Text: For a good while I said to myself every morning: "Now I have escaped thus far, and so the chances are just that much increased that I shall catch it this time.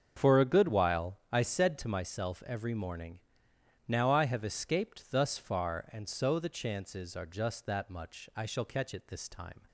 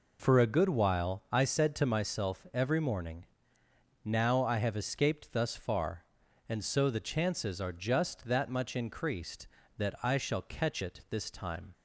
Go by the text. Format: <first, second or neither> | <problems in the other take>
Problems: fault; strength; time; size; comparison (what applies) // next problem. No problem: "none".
second | starts louder than the rest; strong; until 1.1 s; 7 dB // skips "increased that"; at 8.3 s